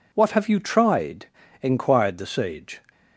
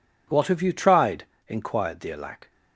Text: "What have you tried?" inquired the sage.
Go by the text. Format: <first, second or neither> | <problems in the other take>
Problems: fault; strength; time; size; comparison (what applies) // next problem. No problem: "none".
first | says "alack" for "sage"; at 2.1 s